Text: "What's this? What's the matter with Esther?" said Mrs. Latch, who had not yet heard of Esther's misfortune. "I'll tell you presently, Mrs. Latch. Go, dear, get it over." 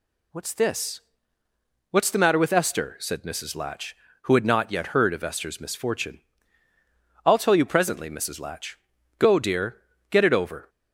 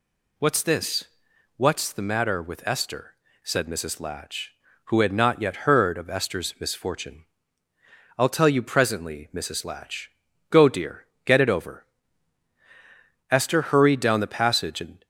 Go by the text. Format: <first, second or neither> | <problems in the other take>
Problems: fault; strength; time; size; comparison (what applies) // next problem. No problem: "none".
first | goes on to say "Esther hurried down the passage and"; strong; from 13.3 s on; 1.7 s long